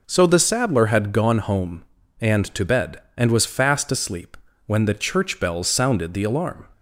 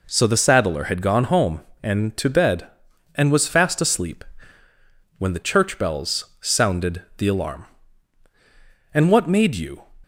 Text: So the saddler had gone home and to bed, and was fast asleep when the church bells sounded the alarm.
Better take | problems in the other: first | pauses between "asleep" and "when"; noticeable; at 4.2 s; 0.96 s long; slight in the first // pauses between "bells" and "sounded"; slight; at 6.2 s; 0.16 s long // goes on to say "And what made you"; noticeable; from 8.9 s on; 0.92 s long

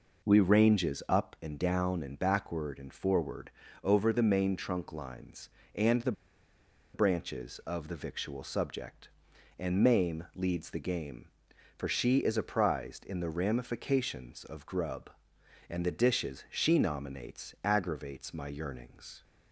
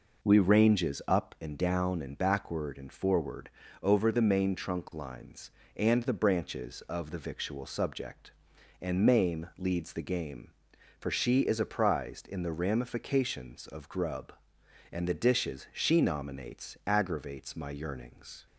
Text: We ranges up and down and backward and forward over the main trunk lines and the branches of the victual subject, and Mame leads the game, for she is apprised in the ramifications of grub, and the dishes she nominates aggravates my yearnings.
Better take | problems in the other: second | pauses between "forward" and "over"; slight; at 3.5 s; 0.32 s long; slight in the second // pauses between "the" and "branches"; noticeable; at 6.1 s; 0.81 s long

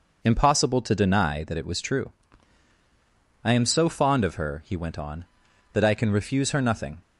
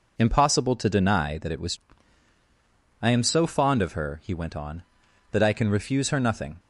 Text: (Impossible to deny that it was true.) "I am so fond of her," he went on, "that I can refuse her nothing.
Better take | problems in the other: first | skips "true"; at 2.3 s

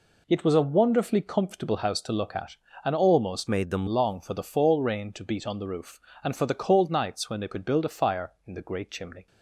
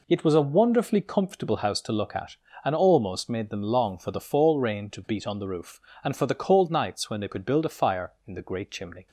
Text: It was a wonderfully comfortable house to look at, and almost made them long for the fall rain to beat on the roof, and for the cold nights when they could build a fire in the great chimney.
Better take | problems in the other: second | changes voice from "made" to "them"; from 3.4 to 3.8 s; 0.4 s long

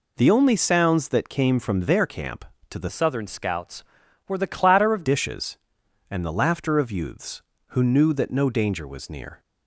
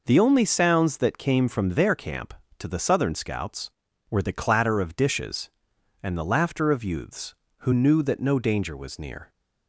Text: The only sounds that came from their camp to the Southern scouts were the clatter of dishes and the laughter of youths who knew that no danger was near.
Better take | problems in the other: second | changes voice from "Southern" to "of"; from 2.8 to 5.0 s; 2.2 s long

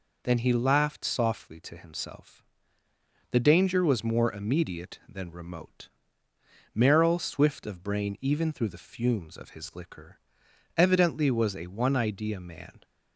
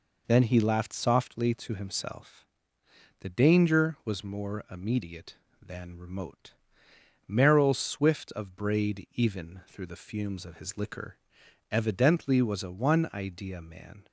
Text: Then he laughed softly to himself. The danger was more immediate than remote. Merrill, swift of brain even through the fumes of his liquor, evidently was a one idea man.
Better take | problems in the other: first | says "braid" for "brain"; at 8.5 s

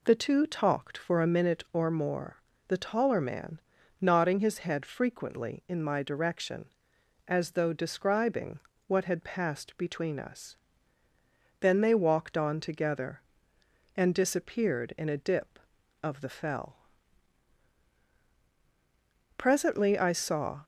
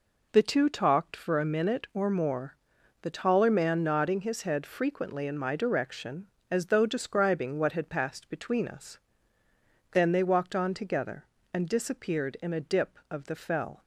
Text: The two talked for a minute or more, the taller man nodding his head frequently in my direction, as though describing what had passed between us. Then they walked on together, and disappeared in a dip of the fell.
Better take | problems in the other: second | pauses between "man" and "nodding"; at 3.5 s; 0.42 s long // pauses between "describing" and "what"; slight; at 8.5 s; 0.26 s long // goes on to say "Presently I saw"; noticeable; from 19.3 s on; 1.2 s long

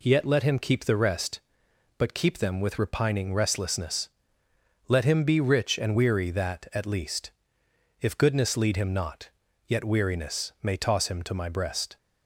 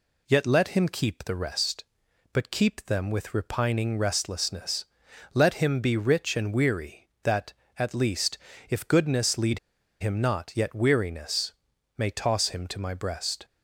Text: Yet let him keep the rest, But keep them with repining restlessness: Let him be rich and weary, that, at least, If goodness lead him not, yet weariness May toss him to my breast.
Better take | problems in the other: first | pauses between "lead" and "him"; at 9.5 s; 0.42 s long // pauses between "weariness" and "May"; at 11.5 s; 0.44 s long

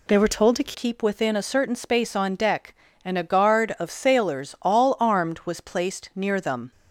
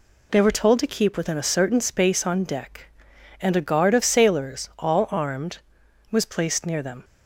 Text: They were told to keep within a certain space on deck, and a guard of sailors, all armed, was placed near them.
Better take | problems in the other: second | changes voice at "keep"; from 0.7 s on; 6.0 s long

